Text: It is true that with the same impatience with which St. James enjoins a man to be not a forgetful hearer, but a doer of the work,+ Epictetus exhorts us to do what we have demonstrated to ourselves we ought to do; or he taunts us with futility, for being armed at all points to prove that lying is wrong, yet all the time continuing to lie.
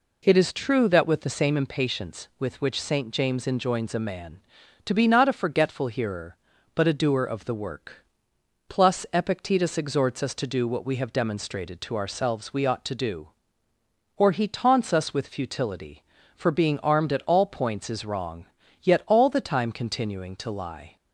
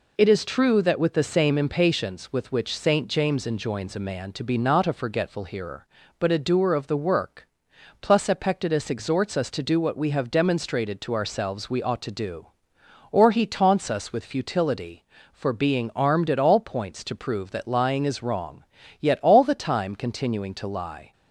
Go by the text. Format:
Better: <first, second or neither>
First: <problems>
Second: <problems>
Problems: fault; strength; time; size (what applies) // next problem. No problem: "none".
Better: second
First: skips "to prove that lying"; at 17.8 s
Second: none